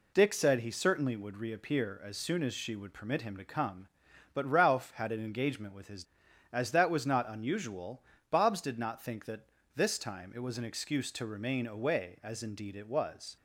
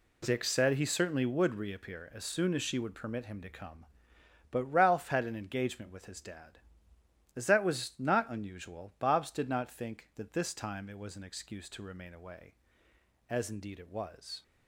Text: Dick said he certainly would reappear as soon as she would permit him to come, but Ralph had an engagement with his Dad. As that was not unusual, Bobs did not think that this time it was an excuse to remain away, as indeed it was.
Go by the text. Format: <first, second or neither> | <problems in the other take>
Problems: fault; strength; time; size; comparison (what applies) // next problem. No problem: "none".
second | skips "Dad"; at 6.2 s // pauses between "that" and "this"; slight; at 9.4 s; 0.28 s long